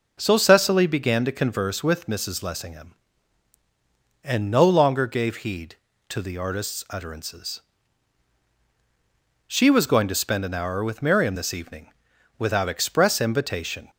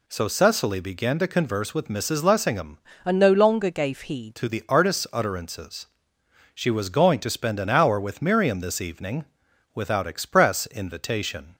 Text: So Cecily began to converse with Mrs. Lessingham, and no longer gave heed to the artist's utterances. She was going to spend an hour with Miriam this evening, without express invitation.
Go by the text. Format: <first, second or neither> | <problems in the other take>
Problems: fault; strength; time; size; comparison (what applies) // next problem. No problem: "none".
first | changes voice from "and" to "heed"; from 3.0 to 4.3 s; 1.3 s long